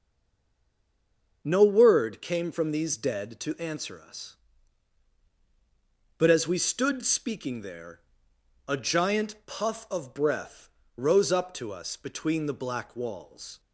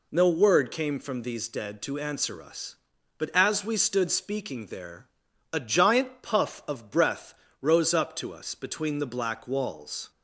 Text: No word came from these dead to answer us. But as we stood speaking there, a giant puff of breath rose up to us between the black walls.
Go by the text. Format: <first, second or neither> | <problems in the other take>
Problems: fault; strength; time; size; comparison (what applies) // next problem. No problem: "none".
second | stays silent before the first word; noticeable; until 1.4 s; 1.4 s long // starts louder than the rest; until 2.4 s; 6.5 dB // pauses between "breath" and "rose"; slight; at 10.6 s; 0.30 s long; slight in the second